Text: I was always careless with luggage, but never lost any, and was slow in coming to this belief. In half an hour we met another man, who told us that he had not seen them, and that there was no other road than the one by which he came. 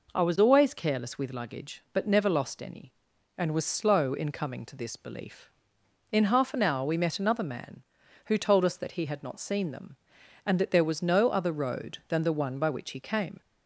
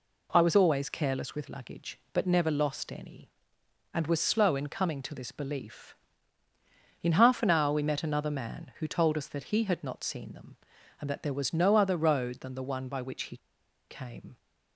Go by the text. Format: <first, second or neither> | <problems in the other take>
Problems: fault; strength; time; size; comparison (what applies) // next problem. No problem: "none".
first | pauses between "he" and "came"; noticeable; at 13.3 s; 0.52 s long